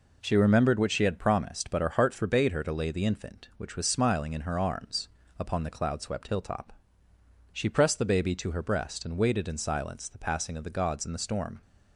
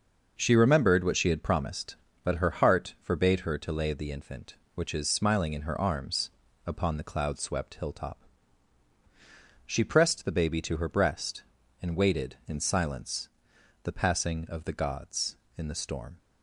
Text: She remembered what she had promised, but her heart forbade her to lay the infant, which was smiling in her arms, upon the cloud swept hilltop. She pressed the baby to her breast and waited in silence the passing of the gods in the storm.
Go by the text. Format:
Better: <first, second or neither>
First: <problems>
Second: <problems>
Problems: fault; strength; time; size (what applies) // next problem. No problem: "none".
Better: first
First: none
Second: says "is" for "was"; at 4.9 s // pauses between "silence" and "the"; noticeable; at 13.2 s; 0.54 s long